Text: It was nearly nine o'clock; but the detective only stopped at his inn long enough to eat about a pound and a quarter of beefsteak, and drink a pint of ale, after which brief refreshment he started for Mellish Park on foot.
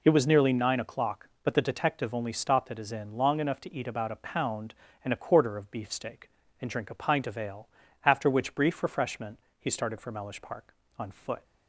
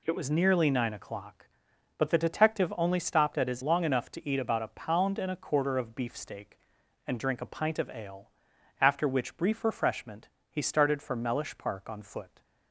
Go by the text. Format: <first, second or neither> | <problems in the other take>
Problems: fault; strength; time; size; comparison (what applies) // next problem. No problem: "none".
first | skips "inn"; at 3.6 s // pauses between "refreshment" and "he"; slight; at 10.2 s; 0.24 s long; slight in the first